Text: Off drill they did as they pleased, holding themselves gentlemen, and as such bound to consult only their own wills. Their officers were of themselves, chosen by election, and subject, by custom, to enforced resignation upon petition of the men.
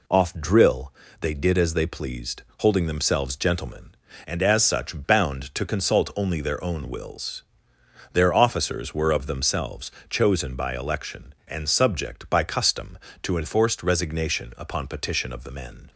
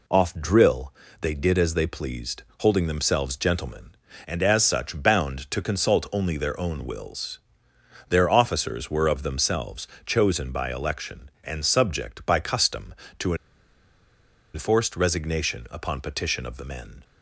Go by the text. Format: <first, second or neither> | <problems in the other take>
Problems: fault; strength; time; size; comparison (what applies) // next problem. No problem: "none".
first | pauses between "drill" and "they"; slight; at 0.9 s; 0.28 s long; slight in the first // pauses between "to" and "enforced"; at 13.3 s; 1.1 s long